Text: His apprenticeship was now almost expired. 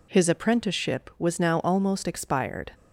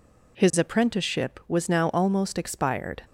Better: neither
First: none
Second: none

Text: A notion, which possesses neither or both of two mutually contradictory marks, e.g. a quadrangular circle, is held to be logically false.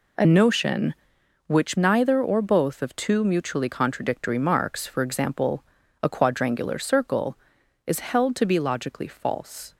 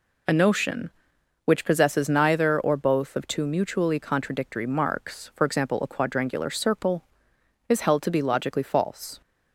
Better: second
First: skips "possesses"; at 1.7 s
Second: none

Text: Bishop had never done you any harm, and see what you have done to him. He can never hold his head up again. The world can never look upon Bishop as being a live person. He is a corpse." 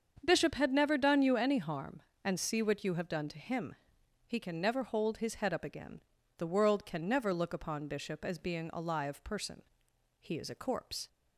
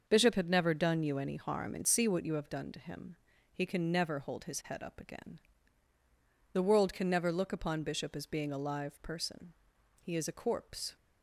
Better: neither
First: starts louder than the rest; until 1.2 s; 7 dB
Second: starts louder than the rest; until 1.0 s; 6.5 dB

